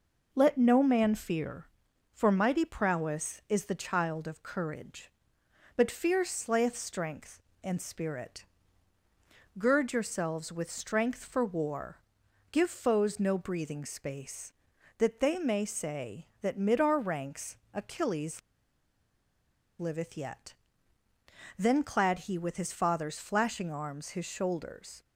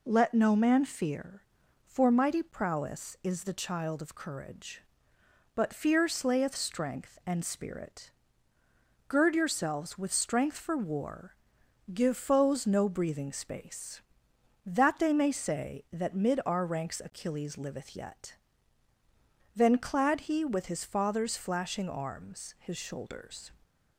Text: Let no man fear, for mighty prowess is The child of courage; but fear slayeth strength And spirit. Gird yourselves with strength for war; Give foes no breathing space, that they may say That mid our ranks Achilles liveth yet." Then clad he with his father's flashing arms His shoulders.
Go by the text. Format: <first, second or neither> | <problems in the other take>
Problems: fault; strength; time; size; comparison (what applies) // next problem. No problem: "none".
second | pauses between "ranks" and "Achilles"; slight; at 17.5 s; 0.16 s long // pauses between "Achilles" and "liveth"; strong; at 18.3 s; 1.3 s long